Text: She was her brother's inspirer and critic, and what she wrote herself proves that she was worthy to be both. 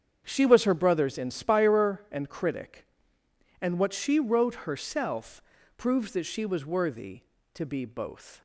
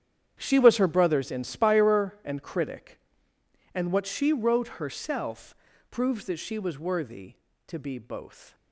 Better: first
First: starts louder than the rest; strong; until 1.2 s; 7.5 dB // pauses between "herself" and "proves"; at 5.3 s; 0.38 s long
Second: gets quieter; strong; throughout; 14.5 dB // starts louder than the rest; strong; until 1.4 s; 9 dB // pauses between "herself" and "proves"; at 5.5 s; 0.38 s long

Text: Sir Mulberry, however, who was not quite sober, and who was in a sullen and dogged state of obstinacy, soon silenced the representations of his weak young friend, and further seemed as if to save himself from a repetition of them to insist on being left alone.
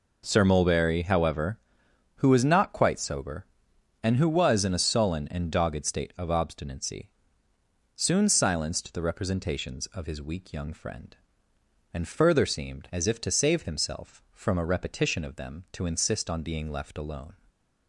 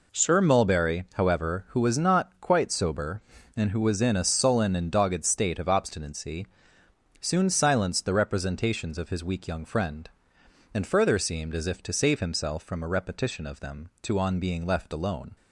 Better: first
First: none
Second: skips "insist"; at 14.1 s

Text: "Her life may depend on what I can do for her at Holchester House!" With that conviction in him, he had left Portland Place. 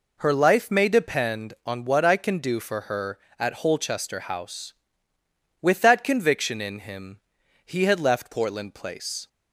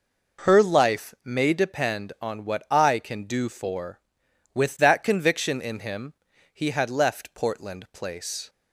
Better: first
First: none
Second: skips "her at Holchester House"; at 4.2 s

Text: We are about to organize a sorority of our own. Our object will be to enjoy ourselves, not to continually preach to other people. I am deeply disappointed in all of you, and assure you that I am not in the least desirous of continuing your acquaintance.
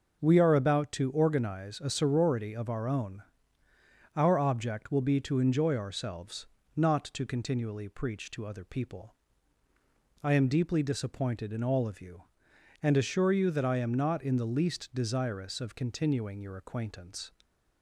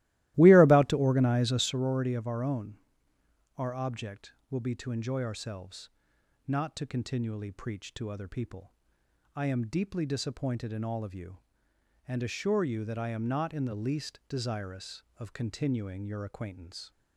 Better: first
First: none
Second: starts louder than the rest; strong; until 1.7 s; 16.5 dB

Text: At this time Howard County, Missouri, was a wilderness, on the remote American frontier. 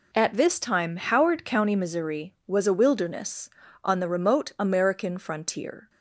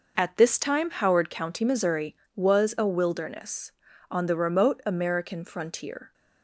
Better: neither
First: none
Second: none

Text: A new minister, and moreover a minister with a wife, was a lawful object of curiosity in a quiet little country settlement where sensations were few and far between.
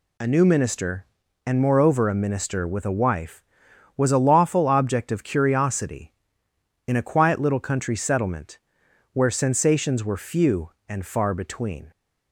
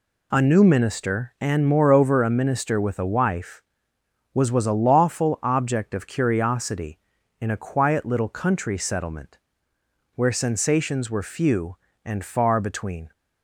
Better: first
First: pauses between "settlement" and "where"; noticeable; at 8.5 s; 0.54 s long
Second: says "was" twice; at 4.4 s // pauses between "settlement" and "where"; noticeable; at 9.3 s; 0.76 s long

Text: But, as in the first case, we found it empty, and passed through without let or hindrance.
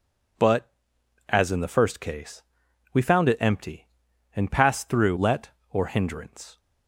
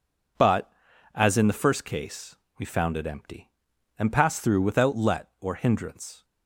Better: second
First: skips "without"; at 5.1 s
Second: none

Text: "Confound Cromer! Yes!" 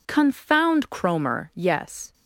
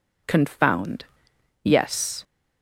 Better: first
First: none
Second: skips "Cromer"; at 1.3 s

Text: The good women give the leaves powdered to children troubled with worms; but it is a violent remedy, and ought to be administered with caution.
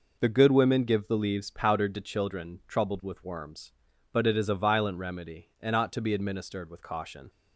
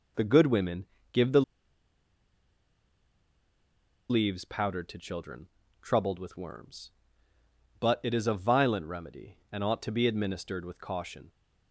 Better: first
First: none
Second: pauses between "women" and "give"; slight; at 0.8 s; 0.26 s long // pauses between "the" and "leaves"; strong; at 1.4 s; 2.6 s long // pauses between "children" and "troubled"; slight; at 5.4 s; 0.36 s long

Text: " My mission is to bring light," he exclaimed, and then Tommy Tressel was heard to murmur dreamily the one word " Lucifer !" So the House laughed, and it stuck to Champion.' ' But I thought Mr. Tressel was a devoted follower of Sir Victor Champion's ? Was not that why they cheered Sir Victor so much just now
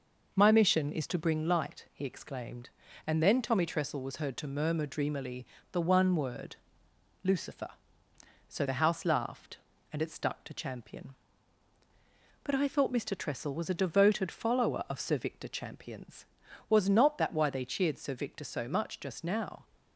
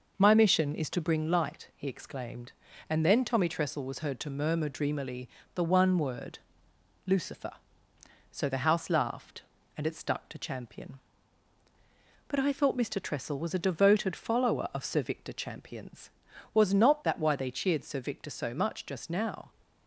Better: neither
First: starts louder than the rest; noticeable; until 1.3 s; 6 dB // pauses between "dreamily" and "the"; slight; at 5.4 s; 0.28 s long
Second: starts louder than the rest; noticeable; until 1.2 s; 6 dB // pauses between "dreamily" and "the"; slight; at 5.2 s; 0.28 s long

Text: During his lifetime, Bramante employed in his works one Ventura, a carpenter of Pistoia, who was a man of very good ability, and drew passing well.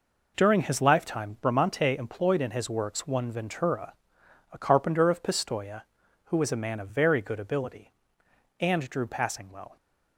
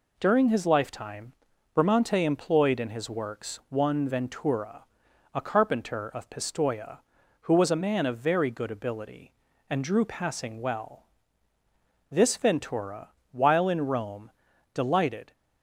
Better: first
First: none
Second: goes on to say "This Ventura while in Rome delighted"; strong; from 12.1 s on; 3.2 s long

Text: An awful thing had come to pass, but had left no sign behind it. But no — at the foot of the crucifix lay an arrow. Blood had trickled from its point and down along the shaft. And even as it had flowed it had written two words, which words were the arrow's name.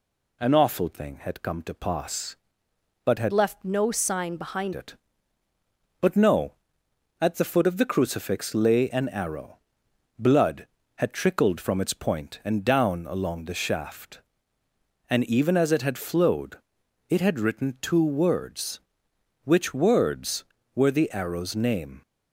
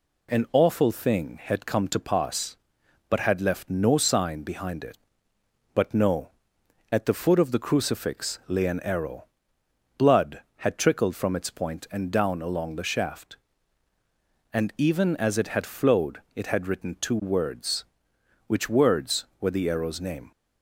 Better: second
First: changes voice from "left" to "behind"; from 3.3 to 4.7 s; 1.4 s long // pauses between "flowed" and "it"; noticeable; at 16.5 s; 0.54 s long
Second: none

